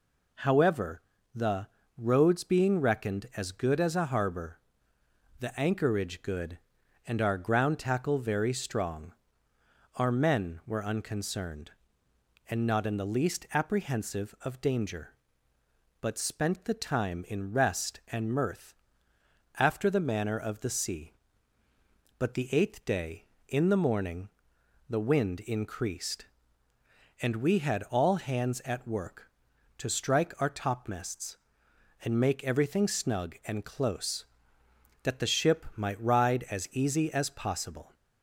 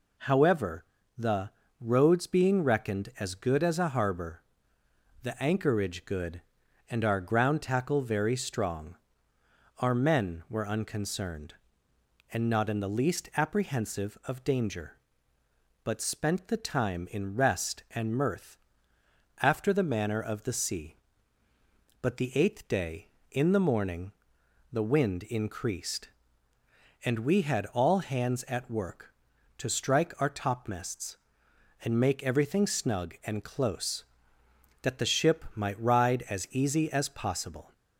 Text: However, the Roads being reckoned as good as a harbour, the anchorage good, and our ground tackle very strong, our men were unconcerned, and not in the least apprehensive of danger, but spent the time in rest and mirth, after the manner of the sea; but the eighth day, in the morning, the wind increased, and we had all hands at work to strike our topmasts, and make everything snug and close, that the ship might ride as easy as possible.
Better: neither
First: pauses between "the" and "Roads"; slight; at 1.6 s; 0.32 s long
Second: pauses between "the" and "Roads"; slight; at 1.4 s; 0.32 s long

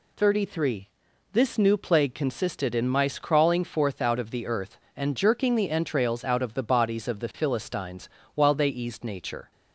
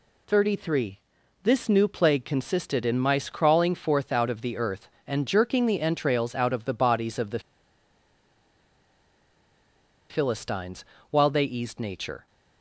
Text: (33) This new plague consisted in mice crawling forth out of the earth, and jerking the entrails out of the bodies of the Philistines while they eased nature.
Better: first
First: pauses between "Philistines" and "while"; slight; at 8.0 s; 0.26 s long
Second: pauses between "the" and "Philistines"; strong; at 7.4 s; 2.6 s long // pauses between "Philistines" and "while"; slight; at 10.8 s; 0.26 s long

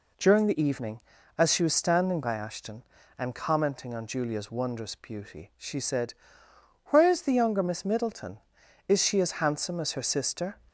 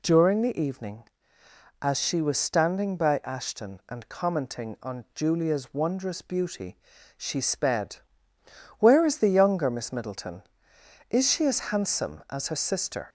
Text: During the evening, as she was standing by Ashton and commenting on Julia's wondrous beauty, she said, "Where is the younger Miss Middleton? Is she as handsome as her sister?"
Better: first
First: none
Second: says "sped" for "said"; at 7.4 s

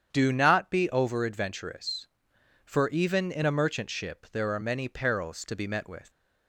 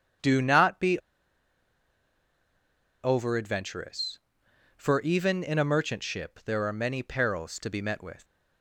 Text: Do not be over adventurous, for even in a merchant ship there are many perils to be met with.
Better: first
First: starts louder than the rest; strong; until 1.1 s; 8.5 dB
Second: starts louder than the rest; strong; until 3.2 s; 8.5 dB // pauses between "be" and "over"; strong; at 0.9 s; 2.0 s long

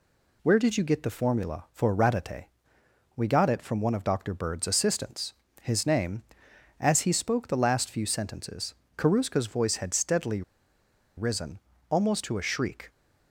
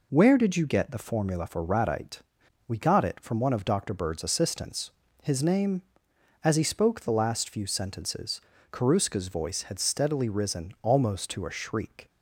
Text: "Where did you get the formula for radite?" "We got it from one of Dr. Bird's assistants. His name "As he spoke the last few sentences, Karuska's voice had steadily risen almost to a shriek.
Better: second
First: pauses between "steadily" and "risen"; noticeable; at 10.4 s; 0.75 s long // pauses between "risen" and "almost"; slight; at 11.5 s; 0.32 s long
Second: none

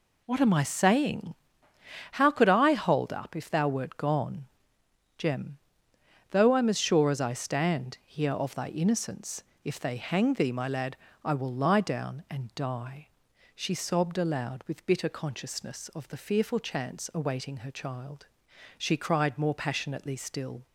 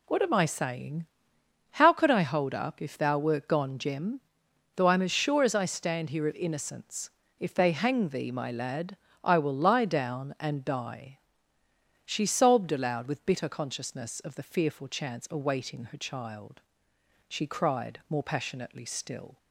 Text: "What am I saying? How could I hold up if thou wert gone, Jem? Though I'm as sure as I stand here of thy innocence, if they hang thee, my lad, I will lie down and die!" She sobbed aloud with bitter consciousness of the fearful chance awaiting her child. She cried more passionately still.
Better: first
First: none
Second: skips "thy"; at 6.3 s

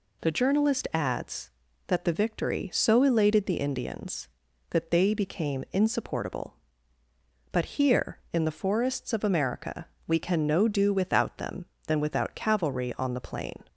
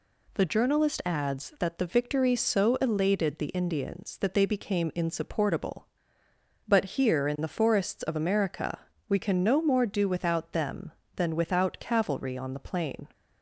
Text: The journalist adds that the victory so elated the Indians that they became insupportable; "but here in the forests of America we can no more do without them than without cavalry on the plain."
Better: second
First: pauses between "America" and "we"; slight; at 9.8 s; 0.20 s long // skips "more"; at 10.6 s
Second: pauses between "America" and "we"; slight; at 8.7 s; 0.30 s long

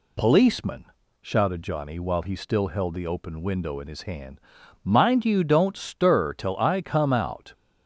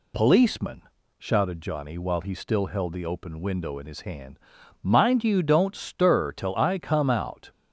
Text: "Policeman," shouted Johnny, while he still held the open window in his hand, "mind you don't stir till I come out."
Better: neither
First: none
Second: none

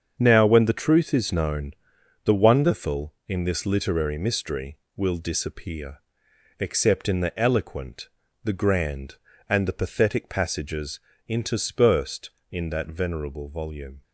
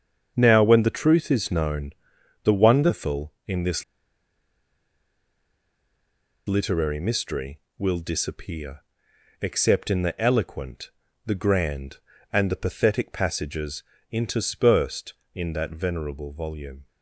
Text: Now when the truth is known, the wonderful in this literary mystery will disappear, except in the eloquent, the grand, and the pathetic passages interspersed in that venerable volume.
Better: first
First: starts louder than the rest; strong; until 1.1 s; 7.5 dB // pauses between "passages" and "interspersed"; slight; at 10.9 s; 0.28 s long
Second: starts louder than the rest; strong; until 1.3 s; 7 dB // pauses between "this" and "literary"; strong; at 3.8 s; 2.6 s long // pauses between "passages" and "interspersed"; slight; at 13.8 s; 0.28 s long

